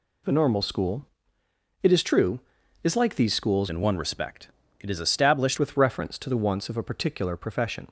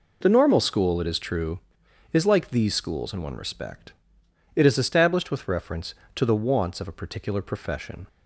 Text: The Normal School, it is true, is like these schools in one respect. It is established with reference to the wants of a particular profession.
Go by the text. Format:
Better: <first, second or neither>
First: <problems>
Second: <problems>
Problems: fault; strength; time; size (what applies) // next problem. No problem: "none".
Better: second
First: changes voice from "in" to "established"; from 3.6 to 5.5 s; 1.9 s long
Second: none